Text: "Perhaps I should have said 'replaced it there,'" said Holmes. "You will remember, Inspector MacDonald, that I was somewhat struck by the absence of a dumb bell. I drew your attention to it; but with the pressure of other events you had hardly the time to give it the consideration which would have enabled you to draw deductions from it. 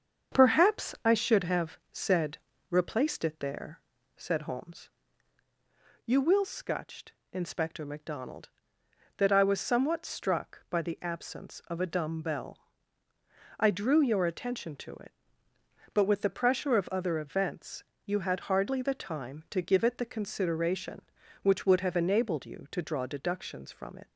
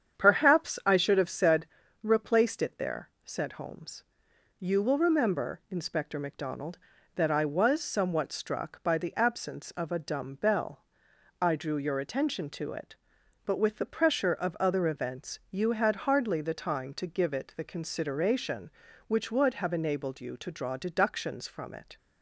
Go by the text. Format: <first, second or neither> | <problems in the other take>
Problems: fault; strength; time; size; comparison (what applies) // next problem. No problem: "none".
second | starts louder than the rest; until 1.4 s; 7 dB; strong in the second // pauses between "said" and "replaced"; slight; at 2.3 s; 0.32 s long; slight in the second // says "scutched" for "remember"; at 6.4 s // pauses between "events" and "you"; slight; at 17.8 s; 0.24 s long